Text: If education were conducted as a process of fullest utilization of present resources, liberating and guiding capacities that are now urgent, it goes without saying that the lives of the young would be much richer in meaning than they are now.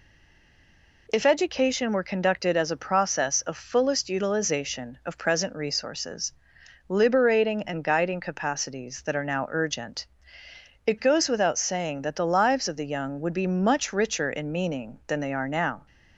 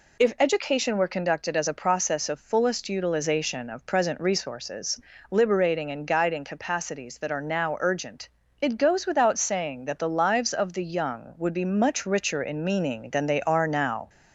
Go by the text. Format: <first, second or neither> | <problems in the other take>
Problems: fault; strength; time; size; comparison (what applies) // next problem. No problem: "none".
second | stays silent before the first word; until 1.0 s; 1.0 s long